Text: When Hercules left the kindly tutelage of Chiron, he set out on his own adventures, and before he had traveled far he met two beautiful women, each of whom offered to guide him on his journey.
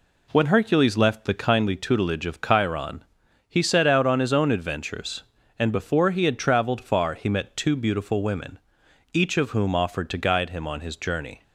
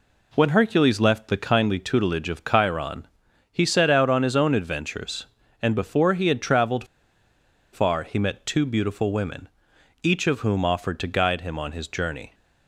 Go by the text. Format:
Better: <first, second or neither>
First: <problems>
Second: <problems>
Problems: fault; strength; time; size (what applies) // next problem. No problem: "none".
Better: first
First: none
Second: pauses between "traveled" and "far"; noticeable; at 6.8 s; 0.88 s long